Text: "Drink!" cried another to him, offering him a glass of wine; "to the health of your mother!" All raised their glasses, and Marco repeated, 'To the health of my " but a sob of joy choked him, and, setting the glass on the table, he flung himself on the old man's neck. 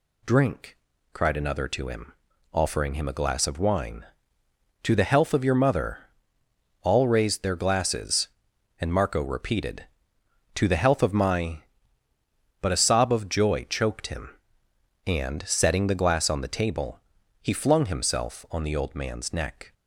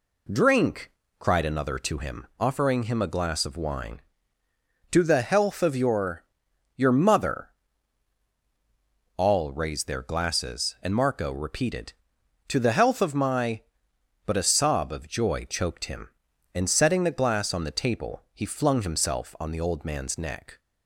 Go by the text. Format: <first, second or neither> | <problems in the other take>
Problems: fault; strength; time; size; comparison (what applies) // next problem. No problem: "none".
first | says "your" twice; at 6.7 s